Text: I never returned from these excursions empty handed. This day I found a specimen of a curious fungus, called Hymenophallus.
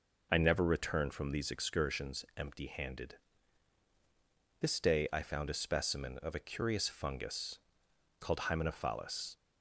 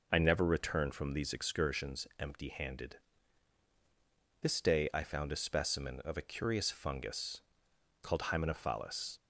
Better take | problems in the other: neither | none

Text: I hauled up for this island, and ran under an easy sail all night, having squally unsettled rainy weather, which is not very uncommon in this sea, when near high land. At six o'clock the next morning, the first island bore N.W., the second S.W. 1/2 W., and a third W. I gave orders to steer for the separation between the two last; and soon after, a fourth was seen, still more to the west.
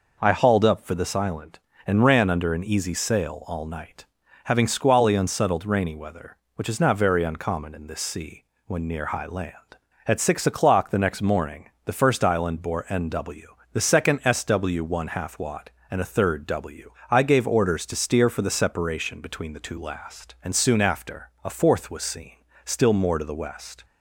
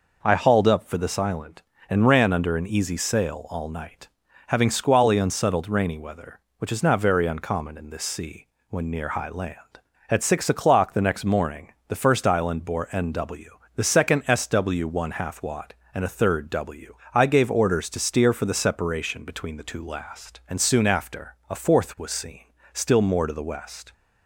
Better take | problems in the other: neither | none

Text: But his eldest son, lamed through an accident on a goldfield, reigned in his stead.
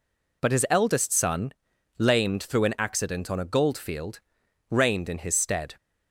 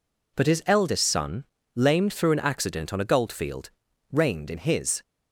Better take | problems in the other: first | stops before "stead"; at 5.0 s

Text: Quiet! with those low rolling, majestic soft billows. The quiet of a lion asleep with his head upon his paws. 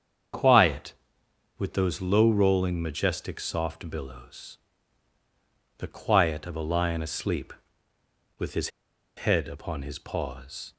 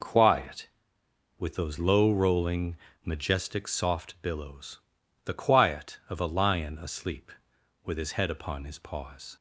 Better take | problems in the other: second | starts louder than the rest; strong; until 1.9 s; 7.5 dB // pauses between "his" and "head"; noticeable; at 8.6 s; 0.54 s long

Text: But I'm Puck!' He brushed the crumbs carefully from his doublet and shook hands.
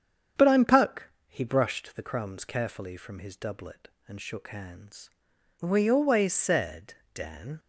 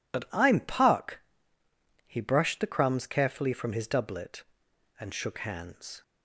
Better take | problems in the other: second | starts louder than the rest; strong; until 1.5 s; 7.5 dB // goes on to say "We always said Dan"; strong; from 5.5 s on; 2.0 s long

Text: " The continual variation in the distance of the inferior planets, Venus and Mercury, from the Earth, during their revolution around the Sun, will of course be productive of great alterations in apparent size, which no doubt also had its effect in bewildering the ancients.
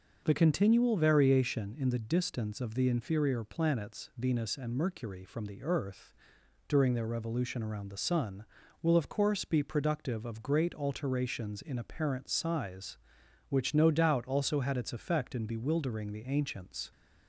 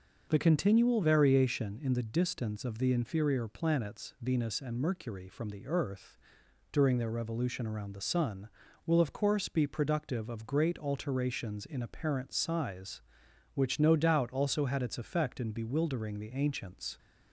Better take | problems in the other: neither | starts louder than the rest; noticeable; the same in both

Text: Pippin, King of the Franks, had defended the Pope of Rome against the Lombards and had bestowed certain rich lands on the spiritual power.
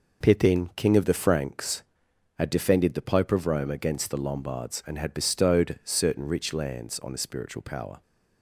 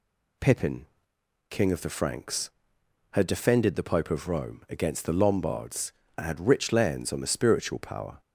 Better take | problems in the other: first | skips "bestowed certain"; at 6.4 s

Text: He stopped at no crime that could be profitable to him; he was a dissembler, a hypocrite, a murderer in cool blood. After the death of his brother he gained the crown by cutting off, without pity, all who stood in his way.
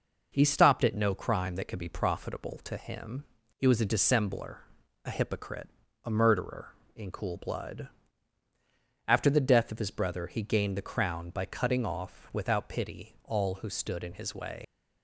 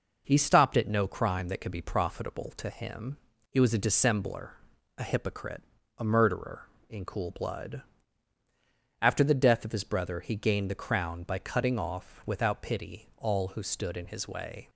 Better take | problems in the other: second | leaves "way" unfinished; at 14.6 s; 110 ms

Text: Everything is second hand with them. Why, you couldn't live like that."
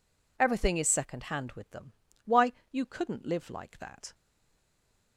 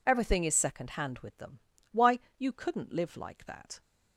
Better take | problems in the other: second | stays silent after the last word; from 4.1 s on; 1.0 s long

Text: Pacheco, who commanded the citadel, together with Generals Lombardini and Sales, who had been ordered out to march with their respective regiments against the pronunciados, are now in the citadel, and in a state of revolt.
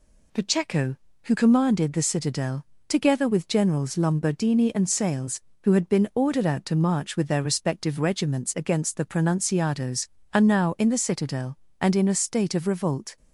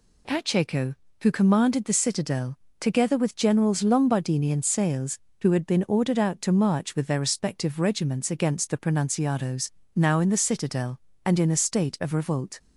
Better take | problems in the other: first | skips "are"; at 9.8 s

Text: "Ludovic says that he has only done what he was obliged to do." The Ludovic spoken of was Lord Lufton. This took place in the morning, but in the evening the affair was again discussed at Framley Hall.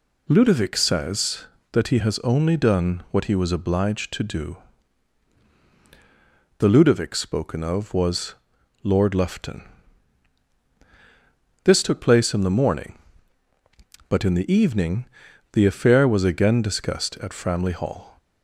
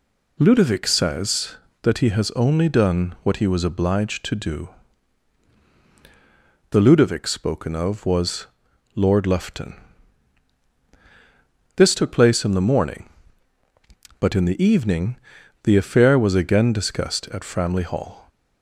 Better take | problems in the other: neither | pauses between "was" and "Lord"; noticeable; the same in both // pauses between "evening" and "the"; noticeable; the same in both

